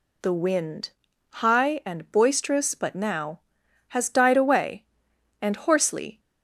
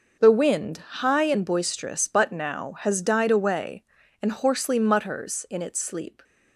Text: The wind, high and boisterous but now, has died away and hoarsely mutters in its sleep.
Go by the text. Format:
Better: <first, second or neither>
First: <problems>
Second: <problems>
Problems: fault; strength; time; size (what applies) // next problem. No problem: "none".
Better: second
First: stops before "mutters in its sleep"; at 6.1 s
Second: none